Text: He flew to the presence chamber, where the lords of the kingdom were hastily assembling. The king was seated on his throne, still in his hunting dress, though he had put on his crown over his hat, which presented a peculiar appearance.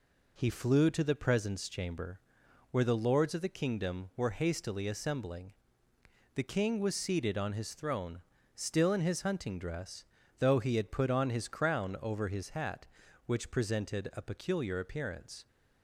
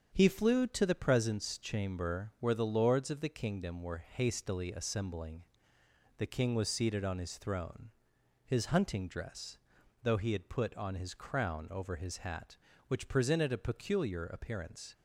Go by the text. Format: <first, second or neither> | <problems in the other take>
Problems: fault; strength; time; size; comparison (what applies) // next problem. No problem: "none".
first | starts louder than the rest; strong; until 1.1 s; 7.5 dB // skips "still in"; at 8.1 s